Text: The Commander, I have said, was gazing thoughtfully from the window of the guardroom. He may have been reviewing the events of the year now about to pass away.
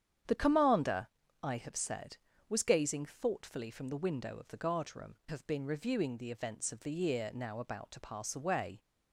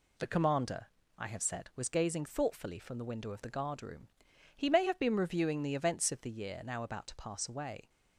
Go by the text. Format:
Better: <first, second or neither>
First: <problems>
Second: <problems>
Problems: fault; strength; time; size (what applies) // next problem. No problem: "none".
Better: second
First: starts louder than the rest; strong; until 1.6 s; 9 dB // skips "He may"; at 5.2 s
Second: none